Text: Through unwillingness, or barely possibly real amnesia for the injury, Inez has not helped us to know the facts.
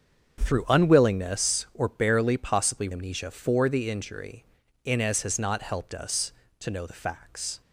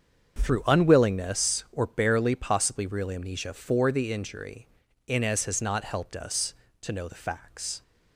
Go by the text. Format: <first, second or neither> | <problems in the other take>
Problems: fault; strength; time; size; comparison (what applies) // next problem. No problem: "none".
second | starts louder than the rest; until 1.4 s; 7 dB; strong in the second // skips "real"; at 2.9 s